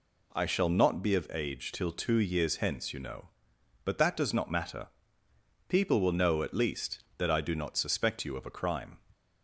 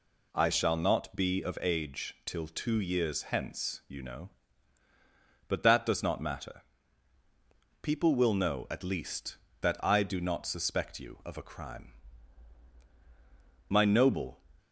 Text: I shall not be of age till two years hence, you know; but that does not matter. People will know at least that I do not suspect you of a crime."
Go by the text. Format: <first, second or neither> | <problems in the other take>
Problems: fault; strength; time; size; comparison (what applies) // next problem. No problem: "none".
first | goes on to say "My noble"; noticeable; from 13.6 s on; 0.72 s long